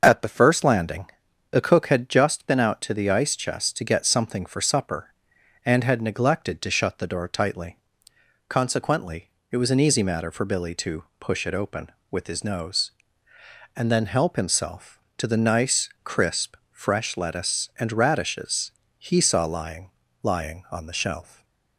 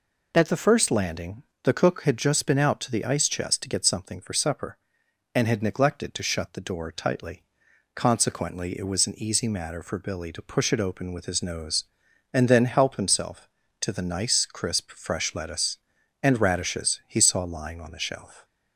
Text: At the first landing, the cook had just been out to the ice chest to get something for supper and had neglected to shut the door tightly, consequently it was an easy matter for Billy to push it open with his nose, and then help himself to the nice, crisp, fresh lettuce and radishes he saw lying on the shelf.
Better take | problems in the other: second | starts louder than the rest; until 1.0 s; 6.5 dB // pauses between "consequently" and "it"; slight; at 9.3 s; 0.20 s long // pauses between "to" and "push"; slight; at 11.0 s; 0.16 s long // pauses between "radishes" and "he"; slight; at 18.7 s; 0.26 s long // says "lying" twice; at 20.2 s // stays silent after the last word; slight; from 21.2 s on; 0.5 s long

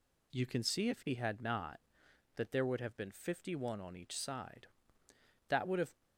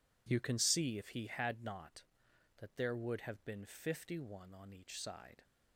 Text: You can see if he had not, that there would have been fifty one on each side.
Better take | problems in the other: second | goes on to say "That would have"; from 5.4 s on; 0.54 s long

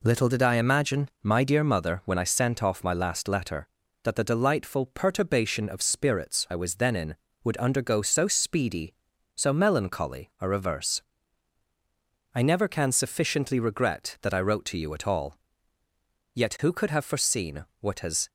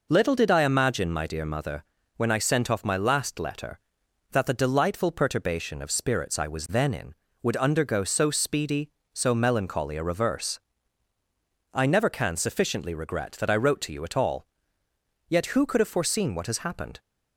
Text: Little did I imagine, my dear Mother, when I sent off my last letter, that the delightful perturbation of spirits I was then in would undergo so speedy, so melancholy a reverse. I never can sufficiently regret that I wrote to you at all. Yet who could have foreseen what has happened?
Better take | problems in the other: second | pauses between "foreseen" and "what"; slight; at 17.6 s; 0.16 s long // stops before "happened"; at 18.2 s

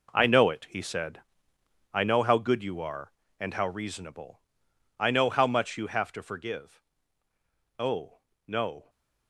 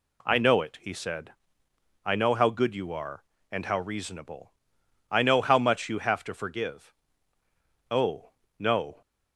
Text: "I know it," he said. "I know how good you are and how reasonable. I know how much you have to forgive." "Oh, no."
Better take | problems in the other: second | gets quieter; strong; throughout; 11.5 dB

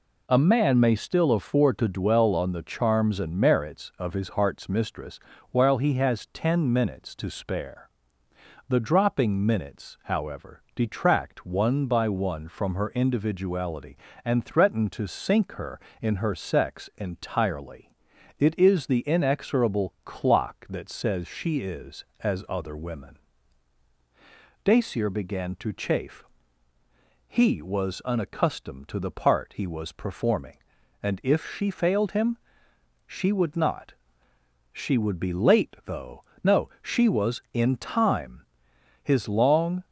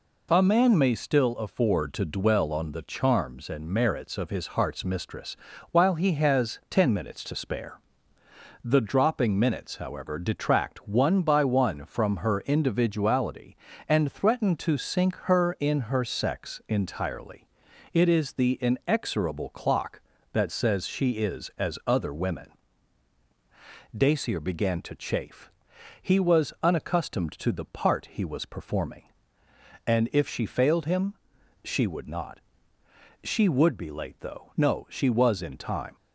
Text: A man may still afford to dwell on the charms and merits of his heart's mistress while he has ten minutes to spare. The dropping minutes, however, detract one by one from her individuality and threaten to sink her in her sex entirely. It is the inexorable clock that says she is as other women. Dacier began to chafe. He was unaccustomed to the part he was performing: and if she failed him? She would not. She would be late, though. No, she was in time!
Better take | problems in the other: second | pauses between "mistress" and "while"; slight; at 5.1 s; 0.32 s long; slight in the second // goes on to say "His long"; noticeable; from 39.0 s on; 0.82 s long

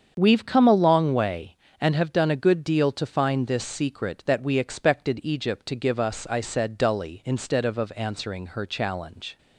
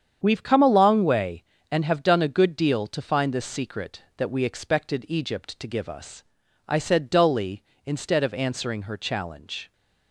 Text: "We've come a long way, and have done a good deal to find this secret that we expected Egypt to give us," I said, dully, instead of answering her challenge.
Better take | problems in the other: second | starts louder than the rest; strong; until 1.1 s; 7.5 dB; strong in the second // says "of" twice; at 7.7 s

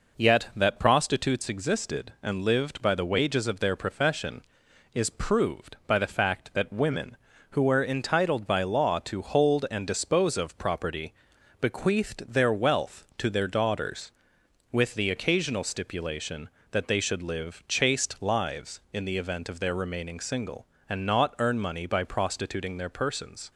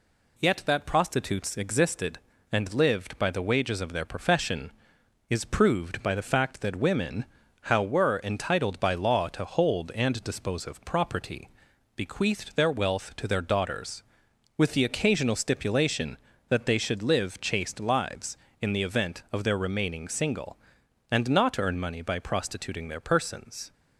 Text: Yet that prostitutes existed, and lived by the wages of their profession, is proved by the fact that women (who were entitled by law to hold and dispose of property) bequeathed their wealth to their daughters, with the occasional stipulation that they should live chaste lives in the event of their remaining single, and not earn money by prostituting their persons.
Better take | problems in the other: first | says "how" for "who"; at 7.6 s

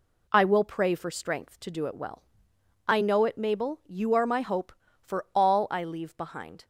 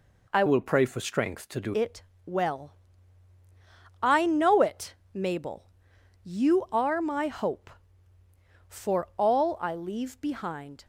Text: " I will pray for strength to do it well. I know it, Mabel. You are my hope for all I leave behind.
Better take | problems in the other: first | changes voice from "will" to "do"; from 0.4 to 1.7 s; 1.3 s long // pauses between "it" and "well"; slight; at 2.0 s; 0.22 s long

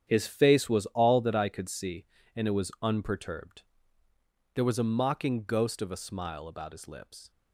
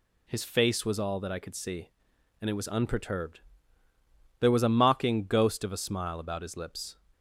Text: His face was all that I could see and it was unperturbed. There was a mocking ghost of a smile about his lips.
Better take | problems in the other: second | gets quieter; strong; throughout; 10 dB

